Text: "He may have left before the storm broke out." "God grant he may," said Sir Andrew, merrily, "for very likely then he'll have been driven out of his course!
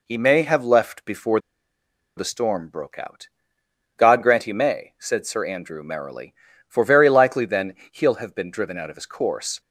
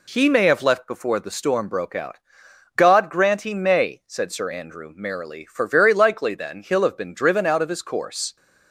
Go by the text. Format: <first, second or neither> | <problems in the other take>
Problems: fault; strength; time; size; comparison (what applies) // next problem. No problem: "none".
second | pauses between "before" and "the"; noticeable; at 1.3 s; 0.79 s long // pauses between "then" and "he'll"; slight; at 7.7 s; 0.16 s long